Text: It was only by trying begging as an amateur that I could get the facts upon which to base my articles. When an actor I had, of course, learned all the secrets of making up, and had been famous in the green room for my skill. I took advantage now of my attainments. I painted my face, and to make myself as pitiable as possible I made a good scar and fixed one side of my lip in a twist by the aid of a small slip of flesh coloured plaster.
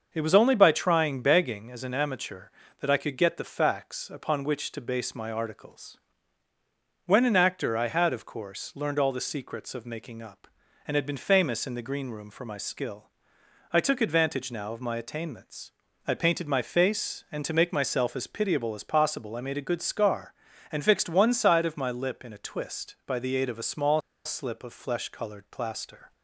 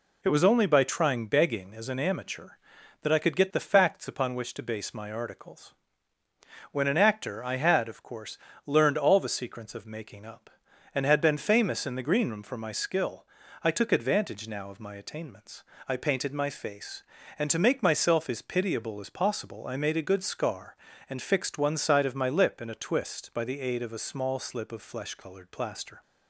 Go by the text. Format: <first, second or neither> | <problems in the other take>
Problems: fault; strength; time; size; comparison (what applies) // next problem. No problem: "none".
second | starts louder than the rest; until 1.1 s; 6.5 dB // pauses between "small" and "slip"; slight; at 24.0 s; 0.24 s long